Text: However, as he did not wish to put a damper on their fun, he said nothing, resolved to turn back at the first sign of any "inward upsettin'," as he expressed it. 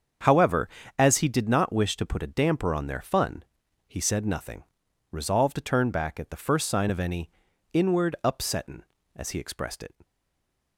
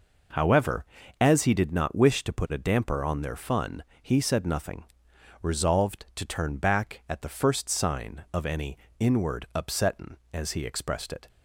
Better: second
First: starts louder than the rest; until 1.5 s; 7 dB // pauses between "any" and "inward"; at 7.2 s; 0.42 s long // stays silent after the last word; slight; from 10.0 s on; 0.7 s long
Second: pauses between "any" and "inward"; slight; at 8.7 s; 0.22 s long

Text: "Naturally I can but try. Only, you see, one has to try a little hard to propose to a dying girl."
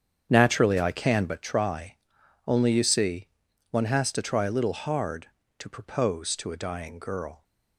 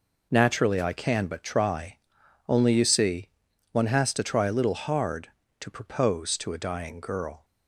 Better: second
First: starts louder than the rest; strong; until 1.5 s; 8 dB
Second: none

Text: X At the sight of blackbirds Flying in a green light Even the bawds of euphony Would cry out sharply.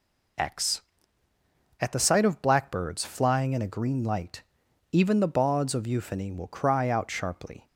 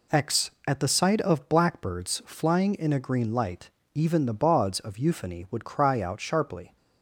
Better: second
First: pauses between "light" and "Even"; noticeable; at 4.4 s; 0.50 s long // says "Will" for "Would"; at 6.3 s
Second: pauses between "light" and "Even"; slight; at 3.6 s; 0.26 s long

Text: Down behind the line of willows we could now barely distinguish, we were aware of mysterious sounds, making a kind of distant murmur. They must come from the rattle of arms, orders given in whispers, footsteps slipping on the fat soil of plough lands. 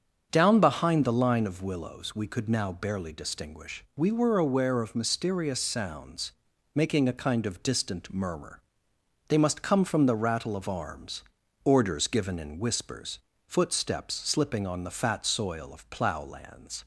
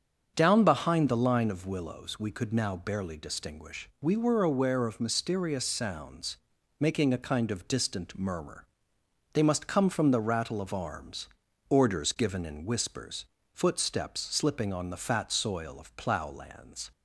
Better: neither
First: starts louder than the rest; strong; until 1.3 s; 7.5 dB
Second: starts louder than the rest; strong; until 1.3 s; 7.5 dB

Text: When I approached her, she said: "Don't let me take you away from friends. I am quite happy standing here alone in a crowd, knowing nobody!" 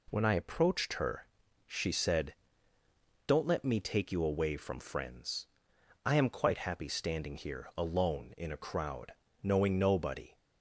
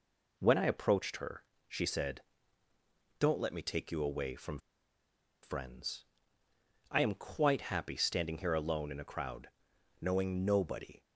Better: first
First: none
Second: pauses between "from" and "friends"; noticeable; at 4.5 s; 0.83 s long

